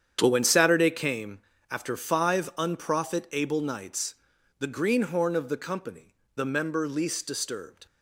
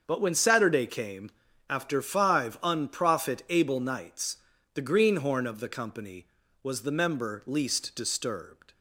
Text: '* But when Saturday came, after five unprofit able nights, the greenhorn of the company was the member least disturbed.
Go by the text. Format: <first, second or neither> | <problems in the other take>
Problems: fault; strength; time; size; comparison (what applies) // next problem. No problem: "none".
second | starts louder than the rest; strong; until 1.2 s; 8.5 dB; also in the second // skips "was"; at 6.2 s